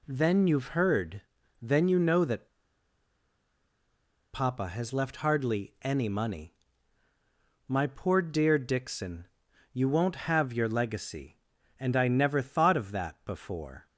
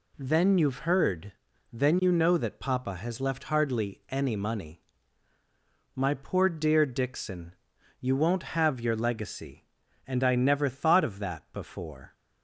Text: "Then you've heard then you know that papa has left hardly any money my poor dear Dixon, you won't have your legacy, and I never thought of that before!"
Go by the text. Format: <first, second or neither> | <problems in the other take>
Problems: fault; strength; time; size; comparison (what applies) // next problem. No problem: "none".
second | pauses between "heard" and "then"; at 1.2 s; 0.40 s long; also in the second // pauses between "that" and "papa"; strong; at 2.4 s; 1.8 s long // pauses between "money" and "my"; at 6.5 s; 1.1 s long; also in the second